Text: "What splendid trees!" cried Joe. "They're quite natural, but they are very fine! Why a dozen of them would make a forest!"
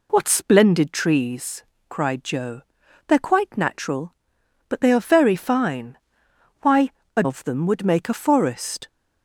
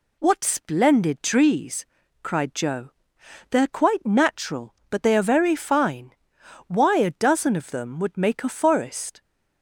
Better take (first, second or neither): second